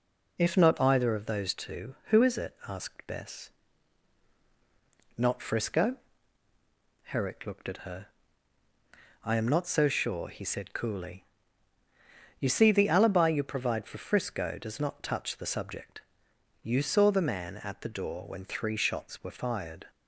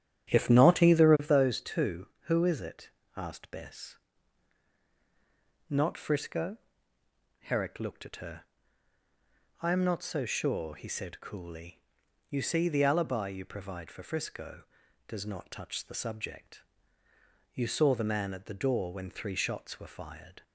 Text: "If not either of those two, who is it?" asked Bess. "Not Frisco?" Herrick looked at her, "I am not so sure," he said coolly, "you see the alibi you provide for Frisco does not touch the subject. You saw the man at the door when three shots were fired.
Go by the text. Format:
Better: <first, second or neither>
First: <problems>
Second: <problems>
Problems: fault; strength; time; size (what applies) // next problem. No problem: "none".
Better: first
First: none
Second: starts louder than the rest; strong; until 1.4 s; 9.5 dB